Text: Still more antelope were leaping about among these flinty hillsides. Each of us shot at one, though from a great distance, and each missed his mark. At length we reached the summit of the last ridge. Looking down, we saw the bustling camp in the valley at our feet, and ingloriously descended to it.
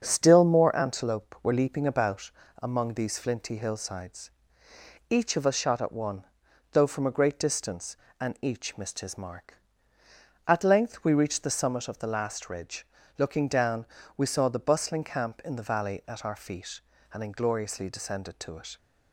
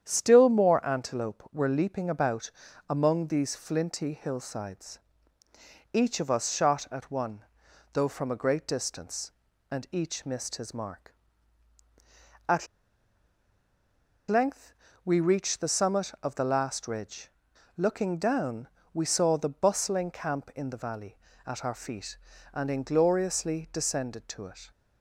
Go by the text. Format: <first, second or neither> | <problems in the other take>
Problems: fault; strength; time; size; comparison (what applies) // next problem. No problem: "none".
first | starts louder than the rest; strong; until 1.0 s; 9 dB; also in the first // pauses between "about" and "among"; at 2.5 s; 0.38 s long; slight in the first // pauses between "At" and "length"; strong; at 12.6 s; 1.6 s long // pauses between "length" and "we"; slight; at 14.7 s; 0.32 s long